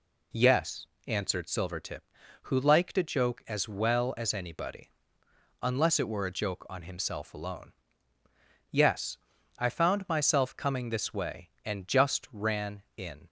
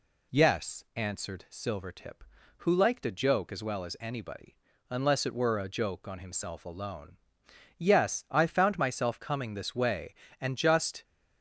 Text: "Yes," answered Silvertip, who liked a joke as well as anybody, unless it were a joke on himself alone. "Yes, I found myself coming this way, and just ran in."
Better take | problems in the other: first | stops before "ran in"; at 11.0 s

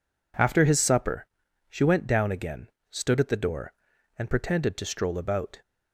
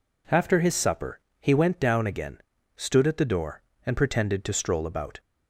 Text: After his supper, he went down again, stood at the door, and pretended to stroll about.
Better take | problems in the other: second | says "she" for "he"; at 1.6 s

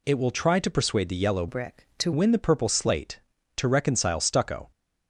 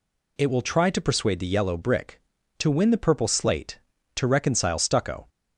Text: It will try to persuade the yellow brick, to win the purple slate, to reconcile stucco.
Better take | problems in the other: second | changes voice from "brick" to "to"; from 1.4 to 2.1 s; 0.7 s long

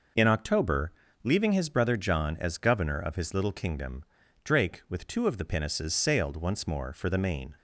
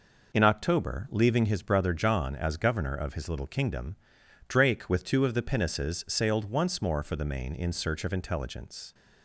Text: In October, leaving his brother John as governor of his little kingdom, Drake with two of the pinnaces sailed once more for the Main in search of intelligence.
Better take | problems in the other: second | stops before "in search of intelligence"; at 7.5 s

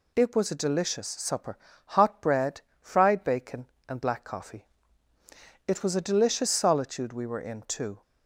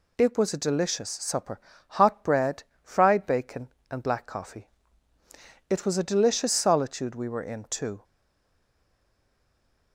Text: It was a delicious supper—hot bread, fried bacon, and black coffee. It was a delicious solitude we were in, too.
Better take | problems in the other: first | stays silent after the last word; noticeable; from 8.0 s on; 1.9 s long

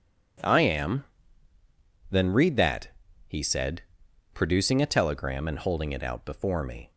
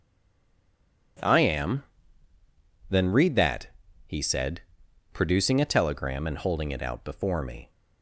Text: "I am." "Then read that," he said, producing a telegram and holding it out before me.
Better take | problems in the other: first | stays silent before the first word; until 1.1 s; 1.1 s long

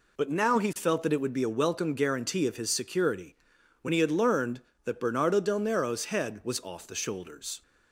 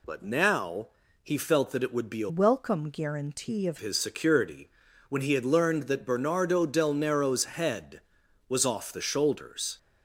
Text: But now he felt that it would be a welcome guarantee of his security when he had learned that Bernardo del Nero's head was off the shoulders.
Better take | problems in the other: first | pauses between "now" and "he"; slight; at 0.8 s; 0.36 s long // changes voice from "welcome" to "of"; from 2.2 to 3.7 s; 1.5 s long // pauses between "security" and "when"; at 4.6 s; 0.40 s long; noticeable in the first

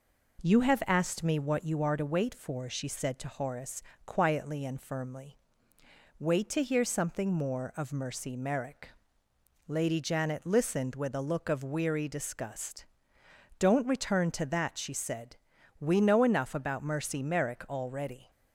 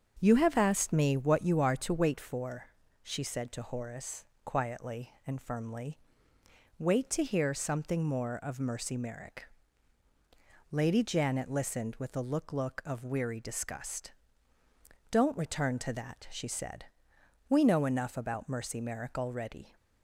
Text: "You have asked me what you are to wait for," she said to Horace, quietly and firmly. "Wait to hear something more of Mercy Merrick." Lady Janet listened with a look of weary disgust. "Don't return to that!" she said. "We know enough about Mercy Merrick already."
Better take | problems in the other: first | starts louder than the rest; until 1.2 s; 7 dB // says "look" twice; at 12.5 s

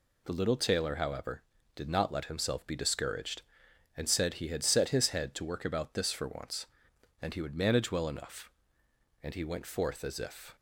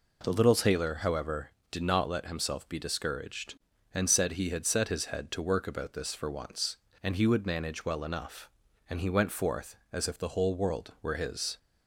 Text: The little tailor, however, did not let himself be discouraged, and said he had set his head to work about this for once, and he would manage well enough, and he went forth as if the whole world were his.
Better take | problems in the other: second | stops before "the whole world were his"; at 10.5 s

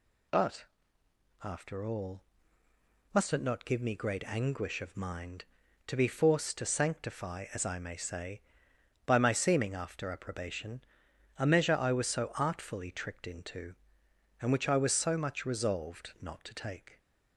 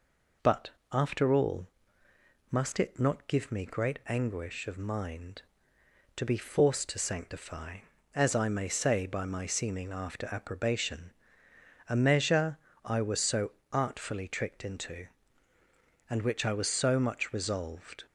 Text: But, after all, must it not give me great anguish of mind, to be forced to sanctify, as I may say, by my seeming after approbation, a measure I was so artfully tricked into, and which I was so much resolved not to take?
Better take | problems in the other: first | pauses between "measure" and "I"; slight; at 12.5 s; 0.28 s long // pauses between "so" and "artfully"; slight; at 13.5 s; 0.20 s long // stops before "not to take"; at 18.0 s

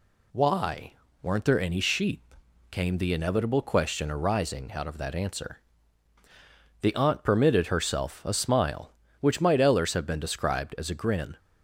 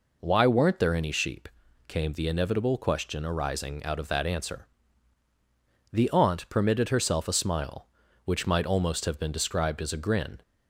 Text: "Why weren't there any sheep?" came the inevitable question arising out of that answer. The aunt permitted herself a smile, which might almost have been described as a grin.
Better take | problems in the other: second | pauses between "Why" and "weren't"; slight; at 0.9 s; 0.30 s long // says "ellers" for "almost"; at 9.6 s

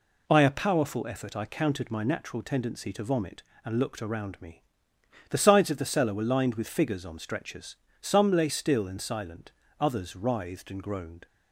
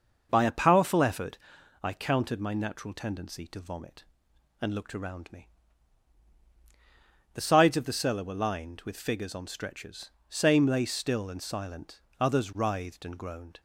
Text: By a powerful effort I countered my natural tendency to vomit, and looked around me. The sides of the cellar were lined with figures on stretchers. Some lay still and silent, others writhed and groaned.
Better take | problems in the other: first | pauses between "effort" and "I"; at 1.3 s; 0.44 s long // says "Same" for "Some"; at 10.2 s

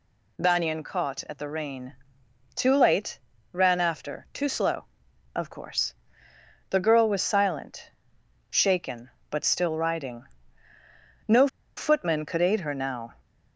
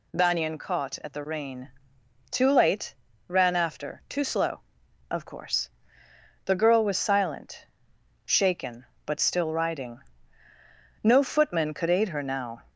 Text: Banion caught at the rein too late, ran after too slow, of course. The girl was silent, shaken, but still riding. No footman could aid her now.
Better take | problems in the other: second | pauses between "rein" and "too"; noticeable; at 1.9 s; 0.60 s long; noticeable in the second // pauses between "No" and "footman"; slight; at 11.4 s; 0.29 s long

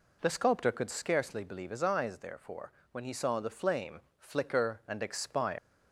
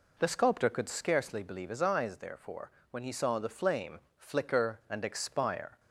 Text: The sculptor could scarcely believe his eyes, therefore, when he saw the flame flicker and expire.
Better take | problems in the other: second | pauses between "flame" and "flicker"; slight; at 3.9 s; 0.18 s long; slight in the second // leaves "expire" unfinished; at 5.5 s; 195 ms

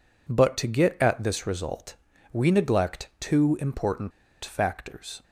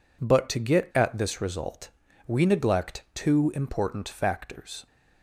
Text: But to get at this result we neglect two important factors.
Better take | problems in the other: second | pauses between "result" and "we"; at 1.9 s; 0.40 s long; also in the second // pauses between "important" and "factors"; slight; at 4.1 s; 0.33 s long

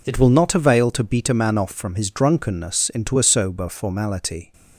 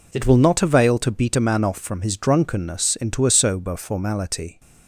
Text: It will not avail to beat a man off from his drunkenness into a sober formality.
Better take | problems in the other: neither | none

